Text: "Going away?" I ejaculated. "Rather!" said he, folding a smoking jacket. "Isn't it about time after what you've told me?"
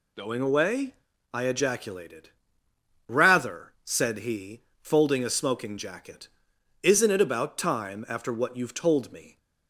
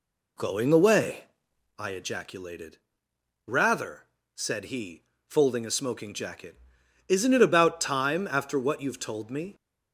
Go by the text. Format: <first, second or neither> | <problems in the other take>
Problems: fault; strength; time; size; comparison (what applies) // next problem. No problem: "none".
first | starts louder than the rest; slight; until 1.7 s; 2.5 dB